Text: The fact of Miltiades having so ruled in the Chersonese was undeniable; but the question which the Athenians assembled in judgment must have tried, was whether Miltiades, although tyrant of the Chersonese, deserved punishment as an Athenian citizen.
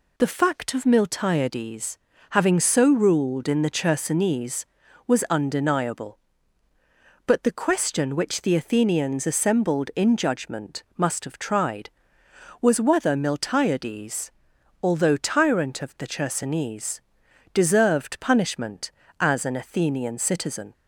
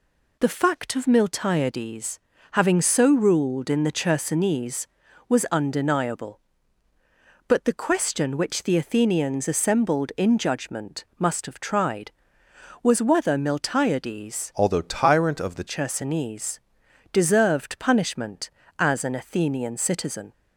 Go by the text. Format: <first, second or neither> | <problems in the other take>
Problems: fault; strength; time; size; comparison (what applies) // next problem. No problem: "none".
first | pauses between "Miltiades" and "having"; slight; at 2.1 s; 0.32 s long; slight in the first // changes voice from "although" to "the"; from 14.5 to 15.6 s; 1.1 s long